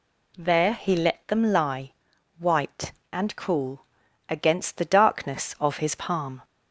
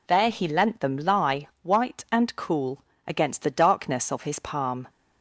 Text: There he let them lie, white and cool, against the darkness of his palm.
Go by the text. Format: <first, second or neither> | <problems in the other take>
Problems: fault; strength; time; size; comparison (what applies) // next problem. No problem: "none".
first | says "lent" for "let"; at 0.4 s